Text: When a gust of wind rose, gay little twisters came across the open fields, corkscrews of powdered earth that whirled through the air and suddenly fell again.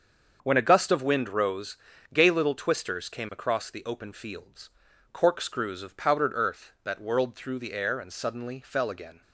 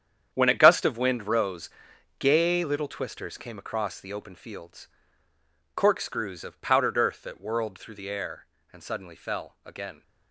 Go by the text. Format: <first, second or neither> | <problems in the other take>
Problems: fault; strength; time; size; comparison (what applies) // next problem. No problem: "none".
first | gets quieter; strong; throughout; 12.5 dB // starts louder than the rest; strong; until 1.3 s; 9 dB; also in the first